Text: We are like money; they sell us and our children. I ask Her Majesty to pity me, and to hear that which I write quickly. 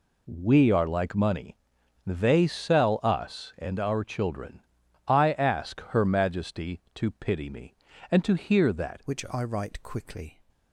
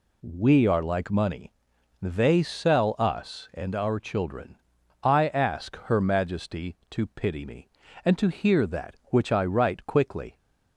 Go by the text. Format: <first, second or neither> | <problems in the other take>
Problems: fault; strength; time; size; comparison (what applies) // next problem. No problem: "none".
second | changes voice at "which"; from 9.0 s on; 1.4 s long